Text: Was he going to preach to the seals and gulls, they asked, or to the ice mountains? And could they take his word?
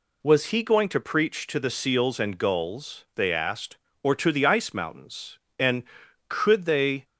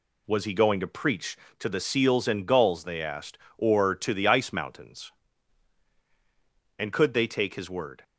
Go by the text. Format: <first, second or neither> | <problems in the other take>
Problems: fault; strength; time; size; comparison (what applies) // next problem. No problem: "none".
second | stops before "take his word"; at 7.0 s